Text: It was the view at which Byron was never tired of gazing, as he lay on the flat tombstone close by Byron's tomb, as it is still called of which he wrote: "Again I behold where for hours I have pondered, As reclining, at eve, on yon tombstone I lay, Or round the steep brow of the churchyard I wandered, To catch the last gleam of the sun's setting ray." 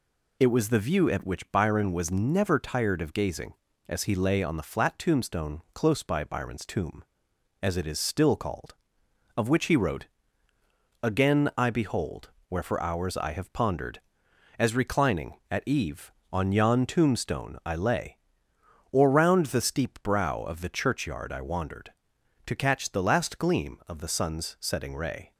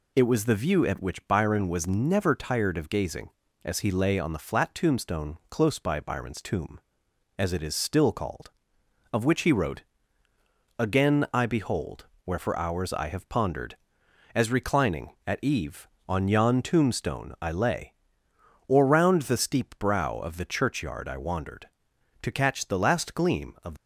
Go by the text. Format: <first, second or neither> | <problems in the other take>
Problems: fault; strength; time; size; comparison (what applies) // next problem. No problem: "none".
first | pauses between "behold" and "where"; slight; at 12.0 s; 0.18 s long; slight in the first // stops before "the sun's setting ray"; at 23.7 s